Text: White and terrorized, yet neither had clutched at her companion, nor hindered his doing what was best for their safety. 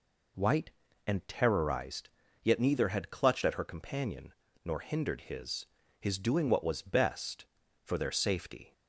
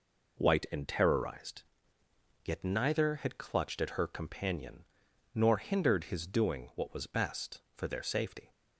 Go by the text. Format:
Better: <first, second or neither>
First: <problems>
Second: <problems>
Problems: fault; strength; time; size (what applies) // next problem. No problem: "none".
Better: second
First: says "his" twice; at 5.9 s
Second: none